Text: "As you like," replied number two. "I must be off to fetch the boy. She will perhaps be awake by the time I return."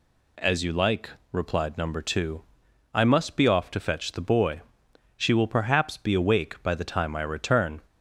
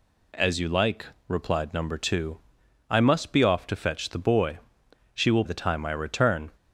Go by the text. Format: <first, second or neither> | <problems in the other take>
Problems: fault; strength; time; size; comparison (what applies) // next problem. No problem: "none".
first | skips "perhaps be awake by"; at 5.4 s